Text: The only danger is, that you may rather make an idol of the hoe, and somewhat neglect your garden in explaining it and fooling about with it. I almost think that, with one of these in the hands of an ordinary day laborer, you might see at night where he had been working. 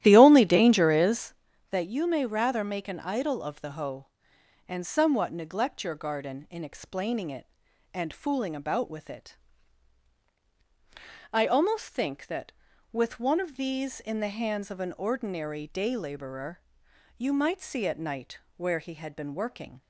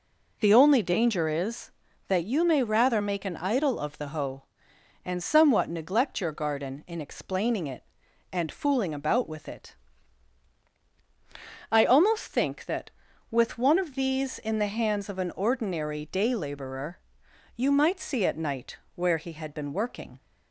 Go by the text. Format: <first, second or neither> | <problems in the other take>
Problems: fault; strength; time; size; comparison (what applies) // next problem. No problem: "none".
second | starts louder than the rest; strong; until 1.4 s; 12.5 dB // pauses between "night" and "where"; slight; at 18.3 s; 0.18 s long; slight in the second